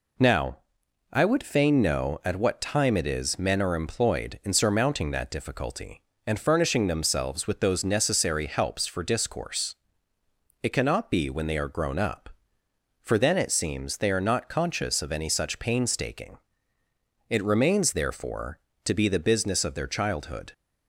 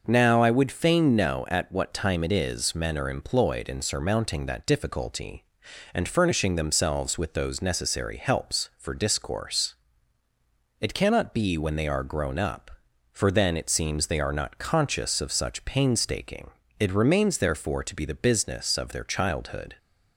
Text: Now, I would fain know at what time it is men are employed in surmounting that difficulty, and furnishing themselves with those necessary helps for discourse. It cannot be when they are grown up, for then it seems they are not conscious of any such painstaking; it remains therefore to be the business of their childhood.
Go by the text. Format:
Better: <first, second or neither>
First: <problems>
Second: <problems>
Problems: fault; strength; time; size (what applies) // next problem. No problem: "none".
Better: first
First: none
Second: skips "any"; at 15.3 s